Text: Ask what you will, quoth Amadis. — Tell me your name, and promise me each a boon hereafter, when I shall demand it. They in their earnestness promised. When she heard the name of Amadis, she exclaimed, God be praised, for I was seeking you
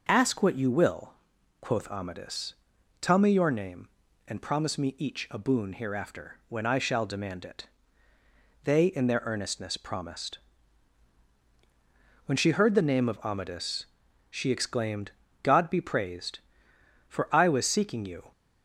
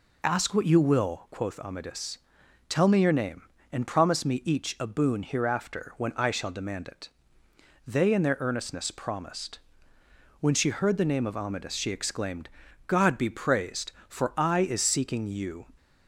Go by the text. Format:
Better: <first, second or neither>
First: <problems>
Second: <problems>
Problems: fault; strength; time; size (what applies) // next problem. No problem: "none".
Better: first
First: none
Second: says "is" for "was"; at 14.5 s